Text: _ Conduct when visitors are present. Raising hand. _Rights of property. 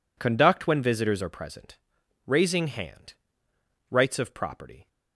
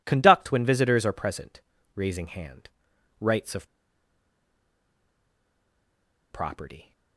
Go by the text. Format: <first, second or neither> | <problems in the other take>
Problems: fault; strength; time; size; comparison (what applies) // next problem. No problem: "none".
first | pauses between "of" and "property"; strong; at 3.6 s; 2.6 s long